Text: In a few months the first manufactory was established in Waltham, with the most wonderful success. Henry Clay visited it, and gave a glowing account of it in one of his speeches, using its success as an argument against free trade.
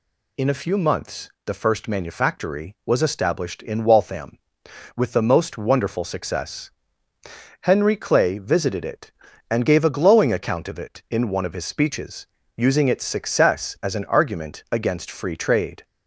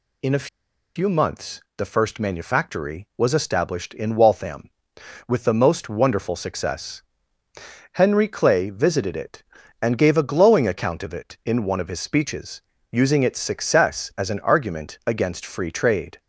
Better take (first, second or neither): first